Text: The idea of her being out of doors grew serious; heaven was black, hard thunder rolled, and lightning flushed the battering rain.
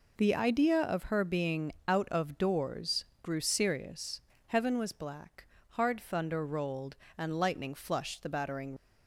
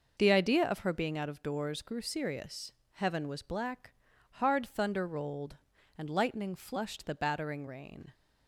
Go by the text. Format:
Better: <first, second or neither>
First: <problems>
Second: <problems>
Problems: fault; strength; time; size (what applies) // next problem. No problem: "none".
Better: second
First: pauses between "being" and "out"; slight; at 1.7 s; 0.16 s long // pauses between "doors" and "grew"; slight; at 3.0 s; 0.18 s long // stops before "rain"; at 8.7 s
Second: none